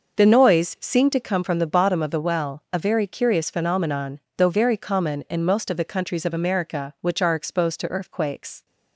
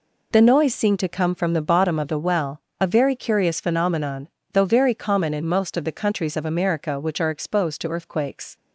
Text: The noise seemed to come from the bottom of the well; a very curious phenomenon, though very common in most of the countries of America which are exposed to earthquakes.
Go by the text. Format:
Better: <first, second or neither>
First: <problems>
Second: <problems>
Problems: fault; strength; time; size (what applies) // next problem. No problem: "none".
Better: second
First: starts louder than the rest; noticeable; until 1.2 s; 6 dB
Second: none